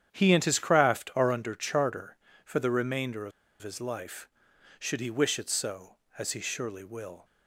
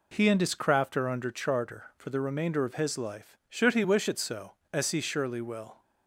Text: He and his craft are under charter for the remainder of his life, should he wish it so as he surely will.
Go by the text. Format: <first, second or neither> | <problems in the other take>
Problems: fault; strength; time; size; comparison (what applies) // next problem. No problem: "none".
second | starts louder than the rest; strong; until 1.1 s; 9.5 dB // pauses between "of" and "his"; slight; at 3.3 s; 0.31 s long